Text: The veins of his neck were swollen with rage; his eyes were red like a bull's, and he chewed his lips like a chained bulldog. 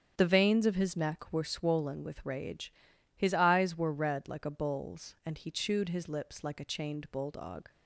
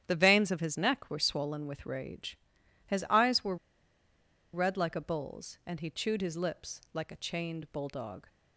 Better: first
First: starts louder than the rest; strong; until 1.1 s; 8 dB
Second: starts louder than the rest; strong; until 1.0 s; 10 dB // pauses between "were" and "red"; noticeable; at 3.5 s; 0.97 s long

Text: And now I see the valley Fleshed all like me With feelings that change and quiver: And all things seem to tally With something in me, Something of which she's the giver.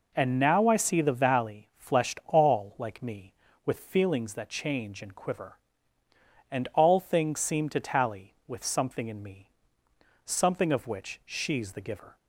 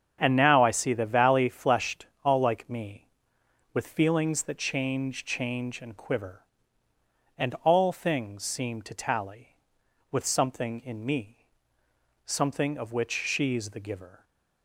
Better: first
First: none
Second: starts louder than the rest; strong; until 1.2 s; 7.5 dB // pauses between "Fleshed" and "all"; slight; at 2.0 s; 0.18 s long // says "change" twice; at 5.2 s

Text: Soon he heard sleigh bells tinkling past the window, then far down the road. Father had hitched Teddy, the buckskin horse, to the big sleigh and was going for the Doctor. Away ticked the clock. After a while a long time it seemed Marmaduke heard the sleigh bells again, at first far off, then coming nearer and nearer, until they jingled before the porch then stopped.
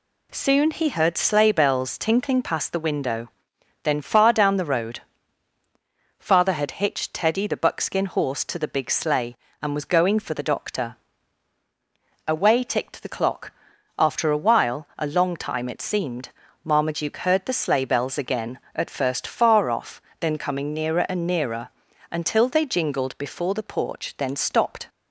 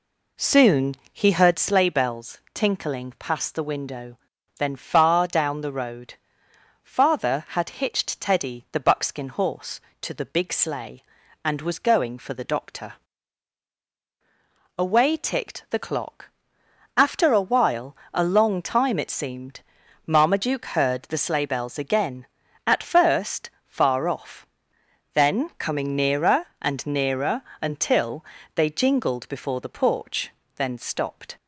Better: first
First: pauses between "seemed" and "Marmaduke"; slight; at 16.2 s; 0.34 s long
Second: starts louder than the rest; slight; until 1.8 s; 3.5 dB // pauses between "Soon" and "he"; slight; at 0.9 s; 0.18 s long // pauses between "while" and "a"; slight; at 17.9 s; 0.16 s long // pauses between "seemed" and "Marmaduke"; noticeable; at 19.6 s; 0.46 s long // pauses between "first" and "far"; slight; at 23.5 s; 0.16 s long // pauses between "until" and "they"; slight; at 28.2 s; 0.30 s long // pauses between "porch" and "then"; slight; at 30.3 s; 0.26 s long

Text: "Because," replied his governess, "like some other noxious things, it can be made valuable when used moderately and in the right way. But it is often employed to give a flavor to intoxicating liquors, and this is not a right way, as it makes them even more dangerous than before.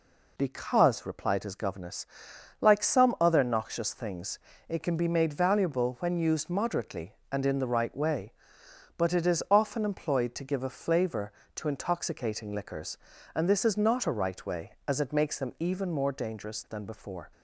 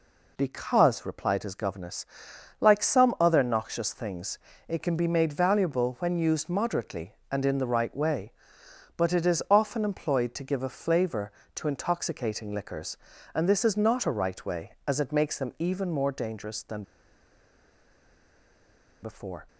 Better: first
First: none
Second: pauses between "than" and "before"; strong; at 16.8 s; 2.1 s long

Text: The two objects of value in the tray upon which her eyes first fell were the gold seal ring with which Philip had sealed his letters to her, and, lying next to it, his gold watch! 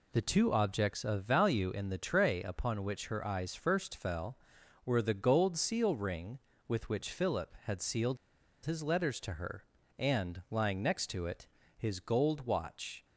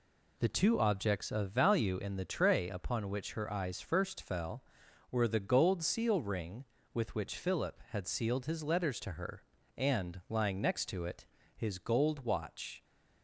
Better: second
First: pauses between "sealed" and "his"; noticeable; at 8.1 s; 0.47 s long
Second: none

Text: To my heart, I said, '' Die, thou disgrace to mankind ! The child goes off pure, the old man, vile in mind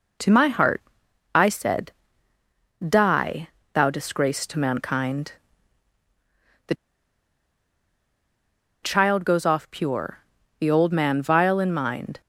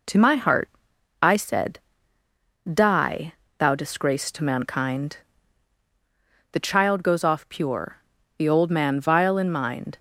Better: second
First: pauses between "The" and "child"; strong; at 6.7 s; 2.0 s long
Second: none

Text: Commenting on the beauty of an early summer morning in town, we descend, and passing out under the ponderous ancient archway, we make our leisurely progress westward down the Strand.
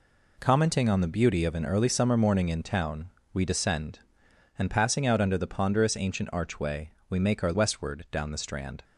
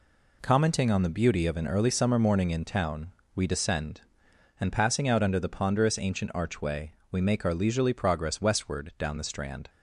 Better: second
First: skips "leisurely progress"; at 7.5 s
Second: none

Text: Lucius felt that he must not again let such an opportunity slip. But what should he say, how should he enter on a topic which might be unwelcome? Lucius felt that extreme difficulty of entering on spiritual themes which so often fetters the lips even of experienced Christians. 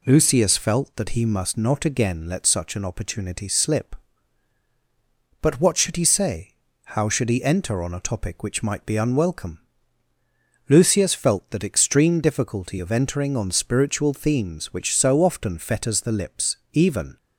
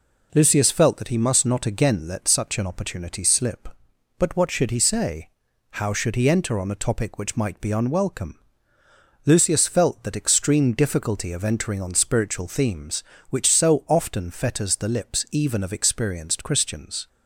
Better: second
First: pauses between "lips" and "even"; slight; at 16.5 s; 0.16 s long // stops before "of experienced Christians"; at 17.1 s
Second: none

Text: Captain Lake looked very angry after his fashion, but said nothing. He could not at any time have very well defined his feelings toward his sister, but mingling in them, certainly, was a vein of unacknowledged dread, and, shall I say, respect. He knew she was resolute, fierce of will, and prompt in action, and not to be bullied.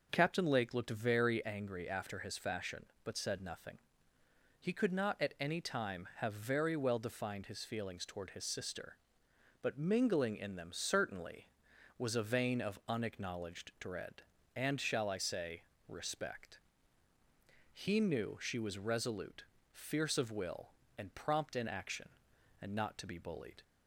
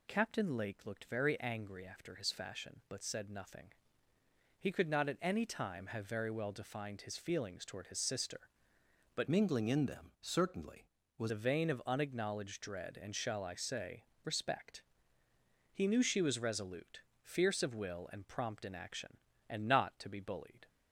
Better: first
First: none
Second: changes voice from "mingling" to "was"; from 9.2 to 11.3 s; 2.1 s long

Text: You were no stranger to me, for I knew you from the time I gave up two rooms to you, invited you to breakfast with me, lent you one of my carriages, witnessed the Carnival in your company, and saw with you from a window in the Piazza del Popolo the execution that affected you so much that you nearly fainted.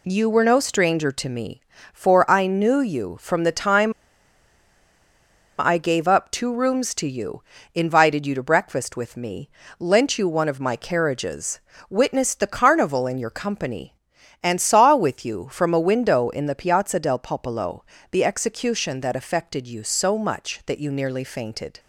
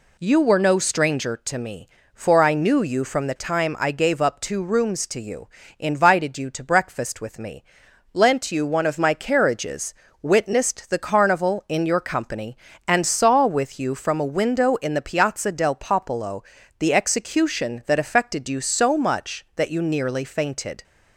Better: second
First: pauses between "time" and "I"; strong; at 3.9 s; 1.6 s long // pauses between "Popolo" and "the"; slight; at 17.8 s; 0.26 s long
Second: pauses between "Popolo" and "the"; slight; at 16.4 s; 0.36 s long

